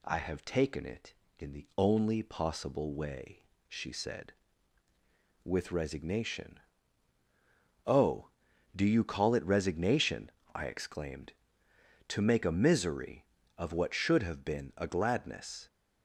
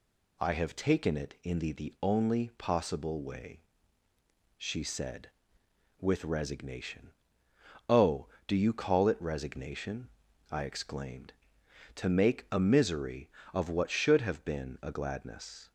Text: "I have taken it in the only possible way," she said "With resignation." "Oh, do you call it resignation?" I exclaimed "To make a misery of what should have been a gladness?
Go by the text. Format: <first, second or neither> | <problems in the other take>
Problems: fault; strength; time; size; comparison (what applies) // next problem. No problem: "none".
first | says "the" twice; at 1.7 s